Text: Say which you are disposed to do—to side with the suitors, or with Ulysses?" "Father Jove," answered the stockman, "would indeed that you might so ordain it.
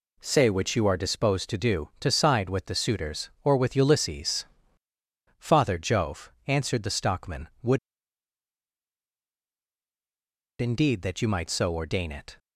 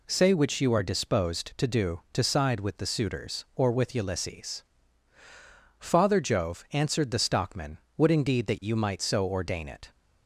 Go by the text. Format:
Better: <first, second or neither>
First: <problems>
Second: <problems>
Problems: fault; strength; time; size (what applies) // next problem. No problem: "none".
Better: second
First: pauses between "would" and "indeed"; strong; at 7.7 s; 2.8 s long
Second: none